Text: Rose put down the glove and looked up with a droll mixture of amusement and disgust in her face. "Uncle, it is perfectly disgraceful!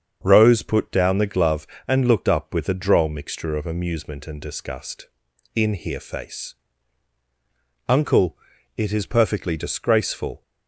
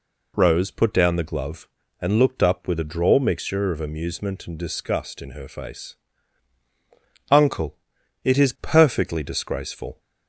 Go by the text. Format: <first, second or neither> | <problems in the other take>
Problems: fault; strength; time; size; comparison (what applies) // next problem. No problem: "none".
second | starts louder than the rest; strong; until 1.2 s; 7 dB // says "here" for "her"; at 5.7 s